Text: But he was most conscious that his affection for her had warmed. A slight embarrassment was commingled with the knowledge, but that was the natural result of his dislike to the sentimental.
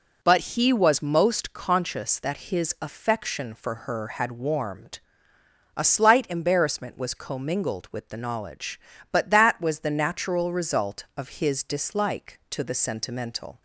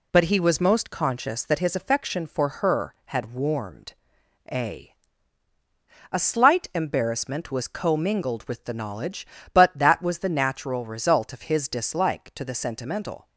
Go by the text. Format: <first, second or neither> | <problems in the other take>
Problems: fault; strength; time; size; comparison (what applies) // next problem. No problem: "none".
first | says "A" twice; at 6.1 s